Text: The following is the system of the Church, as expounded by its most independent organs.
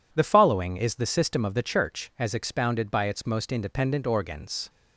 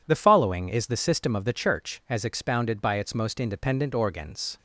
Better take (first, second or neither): neither